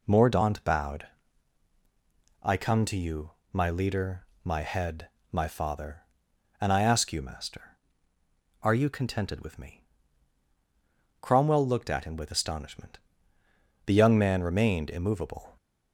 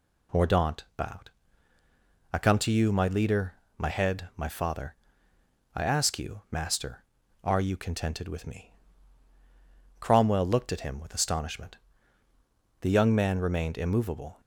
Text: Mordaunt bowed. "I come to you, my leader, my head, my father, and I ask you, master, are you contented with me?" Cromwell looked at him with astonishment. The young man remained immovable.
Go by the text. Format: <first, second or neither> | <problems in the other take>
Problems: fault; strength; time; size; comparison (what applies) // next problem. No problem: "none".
first | skips "and"; at 5.3 s